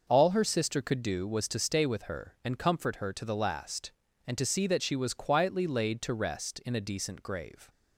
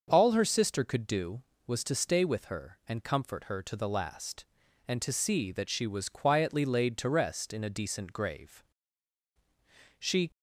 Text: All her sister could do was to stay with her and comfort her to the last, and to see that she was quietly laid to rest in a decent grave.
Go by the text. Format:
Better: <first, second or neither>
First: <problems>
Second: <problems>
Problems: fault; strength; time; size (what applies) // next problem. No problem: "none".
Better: first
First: none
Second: starts louder than the rest; until 1.0 s; 6.5 dB // goes on to say "She"; slight; from 9.9 s on; 0.32 s long